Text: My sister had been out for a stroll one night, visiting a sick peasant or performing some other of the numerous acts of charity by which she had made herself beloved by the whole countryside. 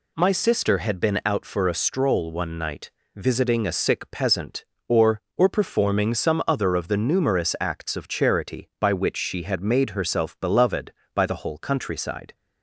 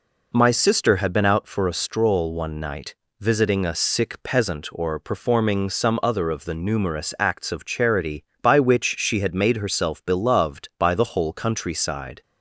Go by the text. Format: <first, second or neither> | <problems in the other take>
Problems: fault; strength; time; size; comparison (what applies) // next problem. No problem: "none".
second | says "or" twice; at 5.3 s